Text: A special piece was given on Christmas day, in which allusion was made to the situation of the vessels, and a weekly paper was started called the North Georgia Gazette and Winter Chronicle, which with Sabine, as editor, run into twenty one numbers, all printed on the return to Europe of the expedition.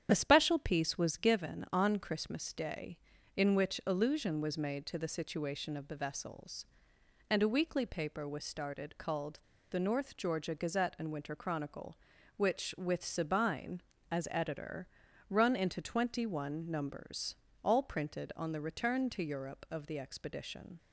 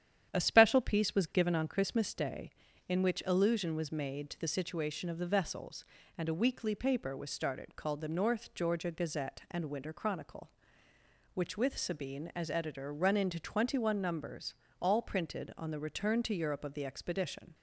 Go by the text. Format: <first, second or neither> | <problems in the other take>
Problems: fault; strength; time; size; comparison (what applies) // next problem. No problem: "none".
second | starts louder than the rest; strong; until 1.1 s; 9 dB; strong in the second // pauses between "called" and "the"; slight; at 9.3 s; 0.32 s long